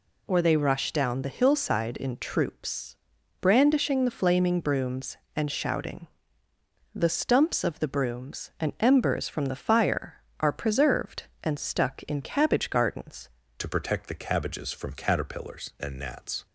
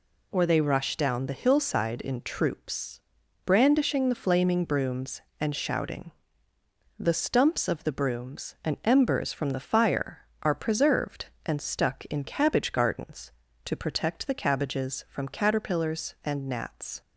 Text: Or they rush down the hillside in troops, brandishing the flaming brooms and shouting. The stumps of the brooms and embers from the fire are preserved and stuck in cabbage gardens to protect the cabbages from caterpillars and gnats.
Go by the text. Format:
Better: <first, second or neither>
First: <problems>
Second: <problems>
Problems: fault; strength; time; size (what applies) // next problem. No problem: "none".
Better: second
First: changes voice at "to"; from 13.5 s on; 2.9 s long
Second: none